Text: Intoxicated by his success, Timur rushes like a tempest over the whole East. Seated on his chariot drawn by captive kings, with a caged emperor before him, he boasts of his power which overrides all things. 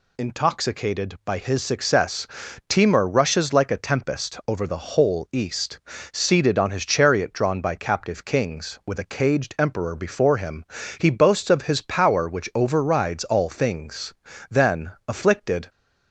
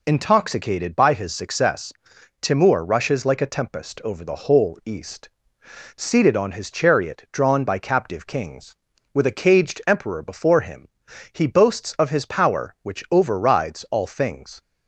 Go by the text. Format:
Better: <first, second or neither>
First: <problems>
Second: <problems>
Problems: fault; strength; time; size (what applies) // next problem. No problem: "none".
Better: second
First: goes on to say "Then afflicted"; noticeable; from 14.4 s on; 1.2 s long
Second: none